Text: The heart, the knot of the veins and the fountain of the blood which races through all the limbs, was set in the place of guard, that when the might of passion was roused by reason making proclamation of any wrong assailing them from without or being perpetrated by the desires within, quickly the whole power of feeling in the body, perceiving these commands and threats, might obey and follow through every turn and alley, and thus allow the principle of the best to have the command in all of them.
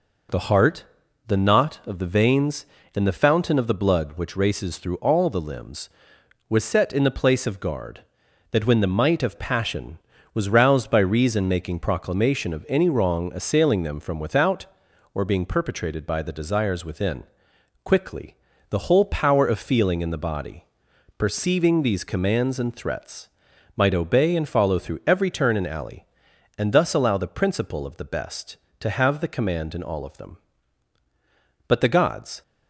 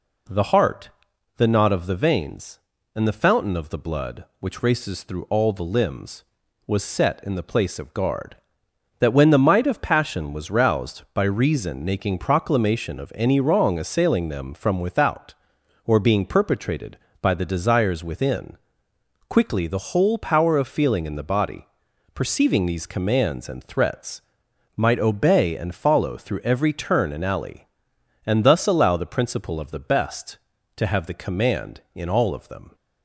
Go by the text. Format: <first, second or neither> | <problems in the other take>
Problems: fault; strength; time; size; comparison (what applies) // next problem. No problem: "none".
second | pauses between "quickly" and "the"; slight; at 18.3 s; 0.34 s long // goes on to say "But the gods"; noticeable; from 31.6 s on; 0.74 s long